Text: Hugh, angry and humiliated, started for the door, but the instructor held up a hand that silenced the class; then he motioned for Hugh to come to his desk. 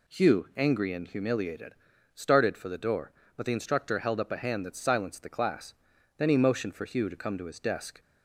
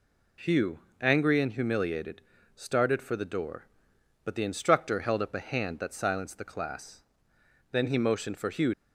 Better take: first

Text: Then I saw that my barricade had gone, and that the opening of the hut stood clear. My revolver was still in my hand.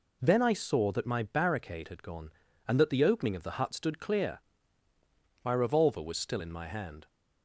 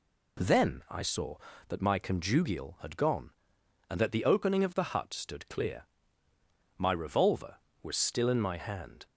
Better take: first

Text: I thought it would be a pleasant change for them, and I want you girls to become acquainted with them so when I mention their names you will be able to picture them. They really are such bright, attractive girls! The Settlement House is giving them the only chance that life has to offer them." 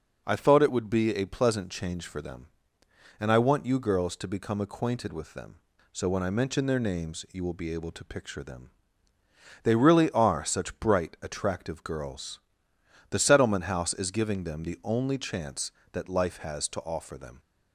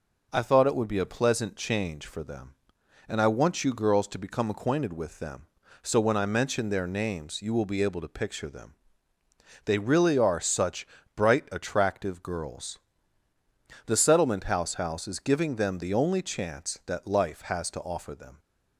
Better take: first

